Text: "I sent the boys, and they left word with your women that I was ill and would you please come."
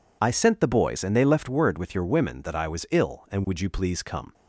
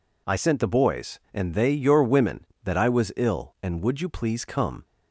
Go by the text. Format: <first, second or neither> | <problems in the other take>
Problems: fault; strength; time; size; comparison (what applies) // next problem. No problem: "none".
first | skips "left word with"; at 1.7 s